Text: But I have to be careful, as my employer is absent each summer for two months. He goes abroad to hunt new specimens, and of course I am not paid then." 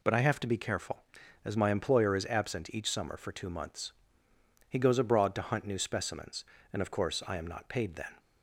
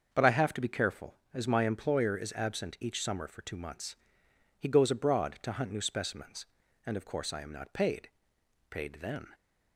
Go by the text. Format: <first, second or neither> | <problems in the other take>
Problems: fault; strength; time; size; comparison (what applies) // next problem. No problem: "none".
first | starts louder than the rest; until 1.1 s; 6.5 dB // says "paid" twice; at 8.6 s